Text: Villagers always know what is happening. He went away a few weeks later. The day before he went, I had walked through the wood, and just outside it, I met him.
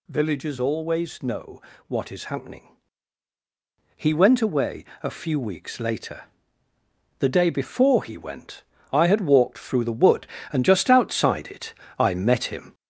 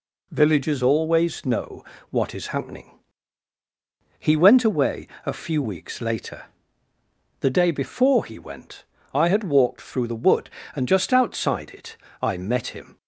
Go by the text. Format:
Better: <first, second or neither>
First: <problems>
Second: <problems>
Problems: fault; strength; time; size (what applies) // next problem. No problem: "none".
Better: second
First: gets louder; noticeable; throughout; 4.5 dB // pauses between "know" and "what"; slight; at 1.6 s; 0.26 s long // pauses between "away" and "a"; slight; at 4.8 s; 0.18 s long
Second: pauses between "know" and "what"; slight; at 1.8 s; 0.26 s long // pauses between "away" and "a"; slight; at 5.0 s; 0.18 s long